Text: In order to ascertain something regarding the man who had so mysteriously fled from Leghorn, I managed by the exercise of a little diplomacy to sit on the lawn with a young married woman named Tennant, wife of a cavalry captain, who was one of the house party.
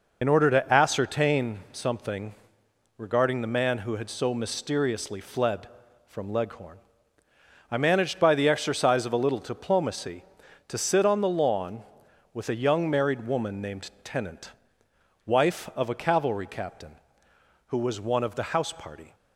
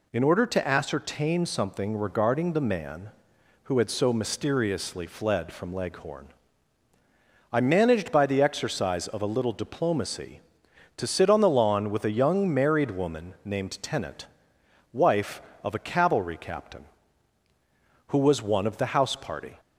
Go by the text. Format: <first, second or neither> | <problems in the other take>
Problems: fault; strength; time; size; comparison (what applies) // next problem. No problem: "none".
second | loses the start of "In"; at 0.2 s; 55 ms // pauses between "something" and "regarding"; noticeable; at 2.3 s; 0.62 s long